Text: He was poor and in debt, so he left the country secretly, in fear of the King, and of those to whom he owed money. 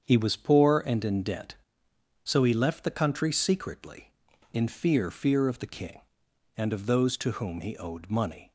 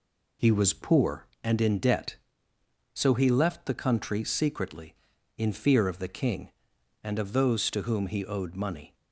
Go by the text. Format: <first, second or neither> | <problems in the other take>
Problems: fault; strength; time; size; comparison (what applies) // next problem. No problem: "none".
second | starts louder than the rest; strong; until 1.0 s; 7.5 dB // says "fear" twice; at 5.0 s